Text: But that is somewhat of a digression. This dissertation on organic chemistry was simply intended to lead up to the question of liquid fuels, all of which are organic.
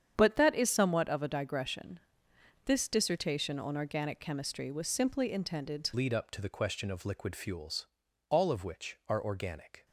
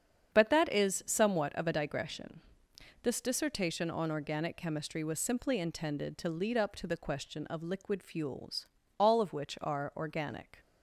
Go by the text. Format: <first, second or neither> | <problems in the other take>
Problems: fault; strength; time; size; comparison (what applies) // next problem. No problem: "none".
second | starts louder than the rest; strong; until 1.1 s; 8.5 dB; strong in the second // changes voice at "lead"; from 5.9 s on; 3.9 s long